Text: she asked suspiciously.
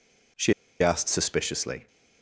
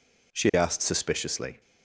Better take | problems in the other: second | pauses between "she" and "asked"; slight; at 0.5 s; 0.29 s long

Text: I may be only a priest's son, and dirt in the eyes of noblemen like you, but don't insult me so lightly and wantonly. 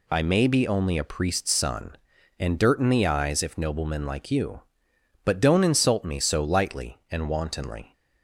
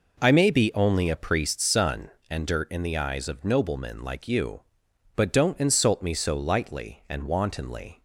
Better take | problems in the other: second | says "if" for "of"; at 3.4 s

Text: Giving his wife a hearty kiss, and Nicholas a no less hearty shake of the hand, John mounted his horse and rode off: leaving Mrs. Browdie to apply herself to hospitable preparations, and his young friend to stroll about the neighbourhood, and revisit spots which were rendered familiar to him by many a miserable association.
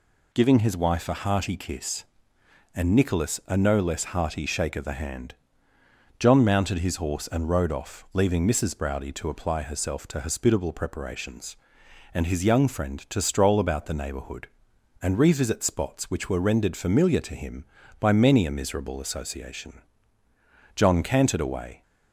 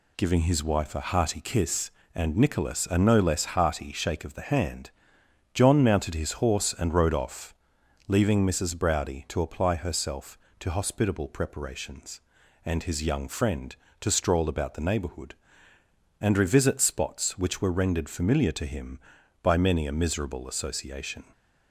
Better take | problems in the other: second | goes on to say "John cantered away"; noticeable; from 20.7 s on; 1.0 s long

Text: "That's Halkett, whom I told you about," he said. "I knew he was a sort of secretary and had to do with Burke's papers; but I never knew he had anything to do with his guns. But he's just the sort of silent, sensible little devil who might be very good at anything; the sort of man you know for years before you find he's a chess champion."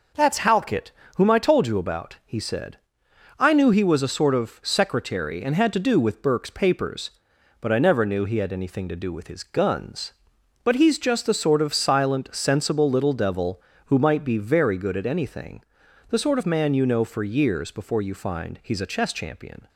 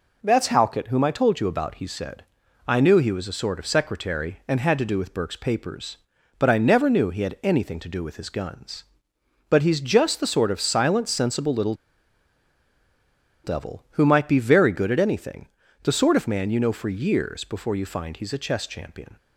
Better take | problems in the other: first | pauses between "little" and "devil"; strong; at 11.7 s; 1.6 s long

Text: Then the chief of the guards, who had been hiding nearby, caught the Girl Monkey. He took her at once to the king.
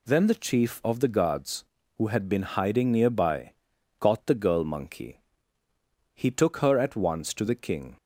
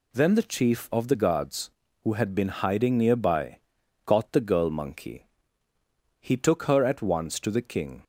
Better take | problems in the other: neither | none

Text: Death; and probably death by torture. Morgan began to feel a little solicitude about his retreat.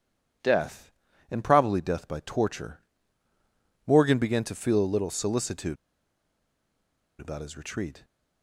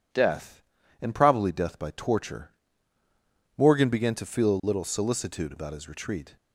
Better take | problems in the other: second | pauses between "solicitude" and "about"; strong; at 5.7 s; 1.4 s long

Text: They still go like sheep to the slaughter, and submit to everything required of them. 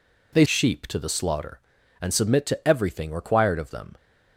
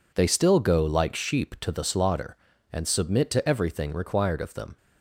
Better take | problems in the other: second | skips "still go like"; at 0.4 s

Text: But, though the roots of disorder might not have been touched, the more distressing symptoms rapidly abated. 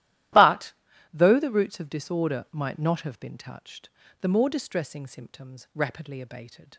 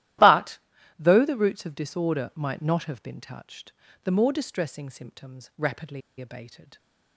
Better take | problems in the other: first | starts louder than the rest; strong; until 1.6 s; 14 dB; strong in the first // pauses between "rapidly" and "abated"; slight; at 6.0 s; 0.19 s long

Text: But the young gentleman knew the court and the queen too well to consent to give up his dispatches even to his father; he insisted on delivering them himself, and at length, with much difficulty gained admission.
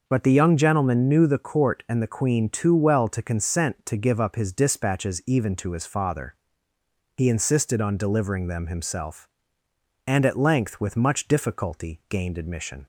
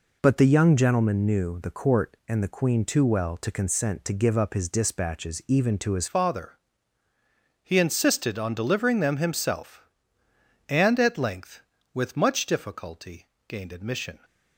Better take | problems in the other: first | changes voice at "father"; from 6.0 s on; 8.1 s long // pauses between "difficulty" and "gained"; slight; at 13.2 s; 0.20 s long

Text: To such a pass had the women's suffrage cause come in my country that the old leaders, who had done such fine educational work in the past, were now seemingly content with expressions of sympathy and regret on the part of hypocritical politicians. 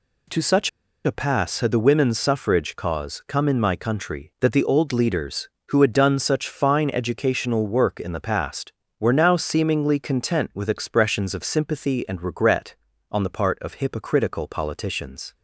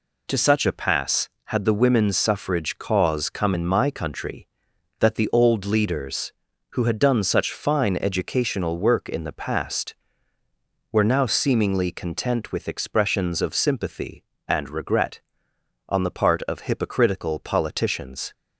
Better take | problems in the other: second | pauses between "such" and "a"; at 0.6 s; 0.36 s long

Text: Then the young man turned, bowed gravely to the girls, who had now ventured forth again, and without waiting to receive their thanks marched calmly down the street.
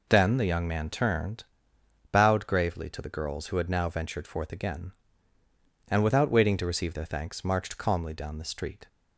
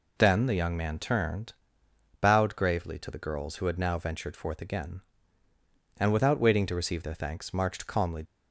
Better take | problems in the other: first | stops before "down the street"; at 8.2 s

